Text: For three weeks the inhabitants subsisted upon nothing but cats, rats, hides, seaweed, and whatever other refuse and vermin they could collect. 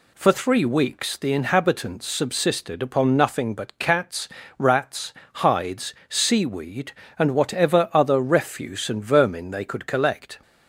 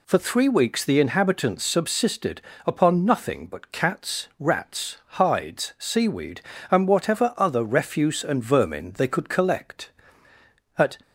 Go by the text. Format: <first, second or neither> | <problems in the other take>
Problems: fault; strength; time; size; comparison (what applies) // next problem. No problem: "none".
first | pauses between "subsisted" and "upon"; slight; at 2.3 s; 0.24 s long // goes on to say "At"; slight; from 10.7 s on; 0.20 s long